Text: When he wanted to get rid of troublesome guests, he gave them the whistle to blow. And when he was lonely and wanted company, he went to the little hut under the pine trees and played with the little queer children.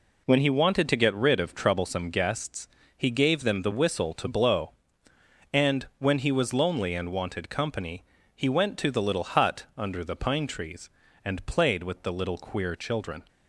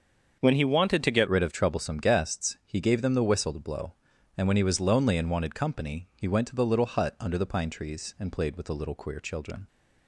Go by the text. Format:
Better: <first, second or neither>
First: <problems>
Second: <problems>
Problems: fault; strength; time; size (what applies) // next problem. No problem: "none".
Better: first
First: none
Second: starts louder than the rest; until 1.4 s; 7 dB // changes voice at "rid"; from 1.2 s on; 8.4 s long